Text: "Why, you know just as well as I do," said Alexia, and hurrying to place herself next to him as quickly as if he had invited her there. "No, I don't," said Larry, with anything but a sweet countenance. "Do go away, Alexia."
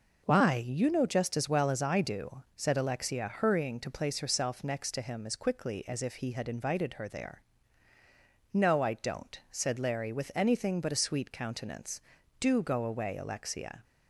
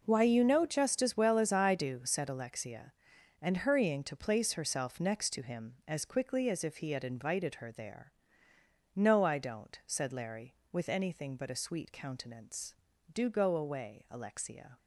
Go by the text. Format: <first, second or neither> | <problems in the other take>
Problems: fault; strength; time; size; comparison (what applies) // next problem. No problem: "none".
second | skips "and"; at 3.2 s